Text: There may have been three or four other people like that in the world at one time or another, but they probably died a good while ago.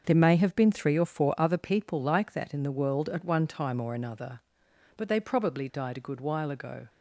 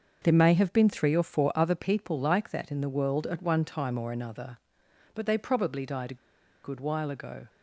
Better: first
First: starts louder than the rest; until 1.0 s; 6.5 dB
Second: starts louder than the rest; until 1.2 s; 6.5 dB // pauses between "a" and "good"; noticeable; at 6.1 s; 0.48 s long

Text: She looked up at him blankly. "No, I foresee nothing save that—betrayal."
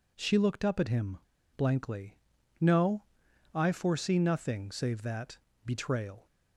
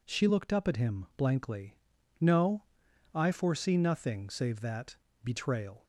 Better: second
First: pauses between "him" and "blankly"; at 1.1 s; 0.38 s long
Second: none

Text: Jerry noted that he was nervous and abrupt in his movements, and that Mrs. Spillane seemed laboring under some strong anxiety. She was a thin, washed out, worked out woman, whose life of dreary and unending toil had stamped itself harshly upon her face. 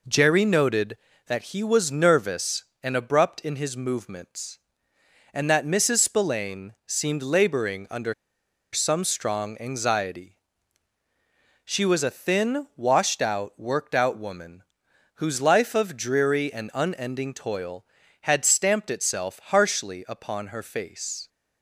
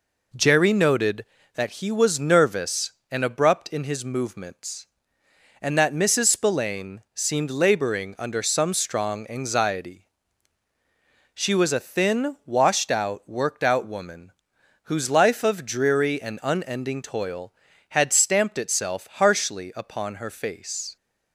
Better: second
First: pauses between "under" and "some"; noticeable; at 8.1 s; 0.59 s long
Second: none

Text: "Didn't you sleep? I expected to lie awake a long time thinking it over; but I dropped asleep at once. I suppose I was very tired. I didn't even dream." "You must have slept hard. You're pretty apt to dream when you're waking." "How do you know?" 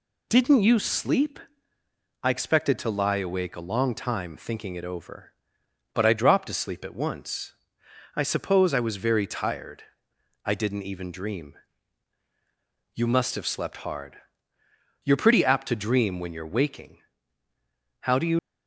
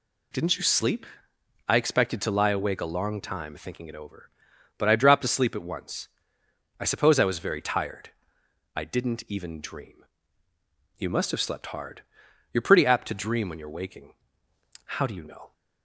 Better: second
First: stops before "know"; at 18.3 s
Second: none

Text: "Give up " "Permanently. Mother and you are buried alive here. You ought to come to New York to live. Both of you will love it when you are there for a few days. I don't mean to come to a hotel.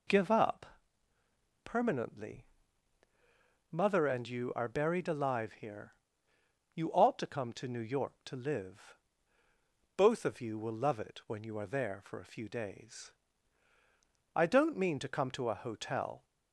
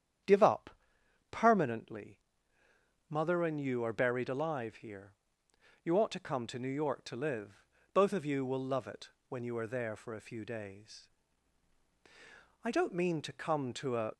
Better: first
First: none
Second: starts louder than the rest; strong; until 1.5 s; 9 dB // pauses between "it" and "when"; slight; at 9.0 s; 0.18 s long // stops before "hotel"; at 14.1 s

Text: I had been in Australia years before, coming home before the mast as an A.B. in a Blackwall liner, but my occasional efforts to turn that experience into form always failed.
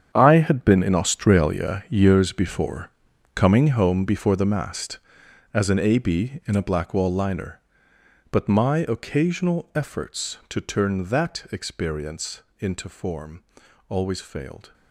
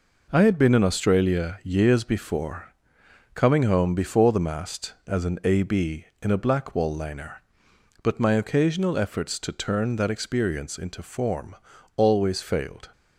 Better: second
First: gets quieter; strong; throughout; 13.5 dB // pauses between "experience" and "into"; slight; at 12.4 s; 0.18 s long // pauses between "form" and "always"; at 13.4 s; 0.44 s long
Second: pauses between "form" and "always"; at 11.5 s; 0.40 s long

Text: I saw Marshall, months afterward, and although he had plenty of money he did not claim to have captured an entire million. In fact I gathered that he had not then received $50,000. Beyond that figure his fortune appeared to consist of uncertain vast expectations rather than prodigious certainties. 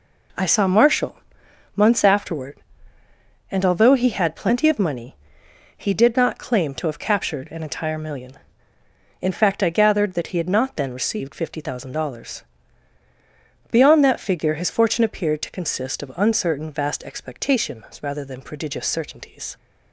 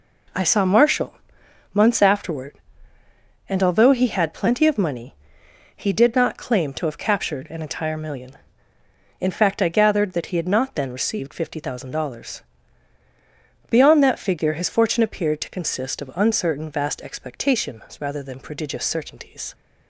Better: neither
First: pauses between "money" and "he"; noticeable; at 5.1 s; 0.60 s long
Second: pauses between "money" and "he"; noticeable; at 5.1 s; 0.60 s long

